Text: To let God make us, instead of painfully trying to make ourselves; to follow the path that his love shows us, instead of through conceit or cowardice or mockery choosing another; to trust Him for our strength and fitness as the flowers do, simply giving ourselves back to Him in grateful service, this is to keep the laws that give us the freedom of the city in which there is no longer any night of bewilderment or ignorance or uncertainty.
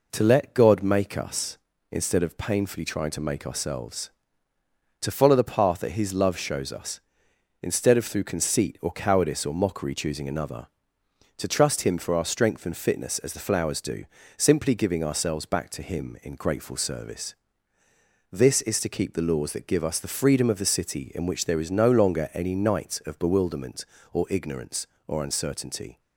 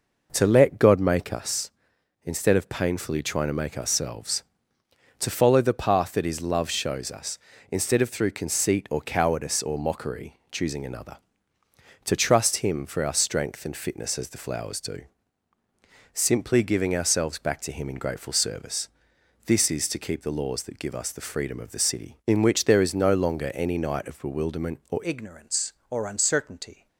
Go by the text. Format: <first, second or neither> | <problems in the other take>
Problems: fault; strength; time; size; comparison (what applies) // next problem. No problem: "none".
first | changes voice at "ignorance"; from 25.0 s on; 1.8 s long